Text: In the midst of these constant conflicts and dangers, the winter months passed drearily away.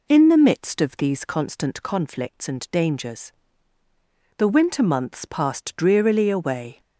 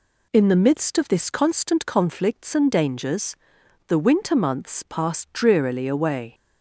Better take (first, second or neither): first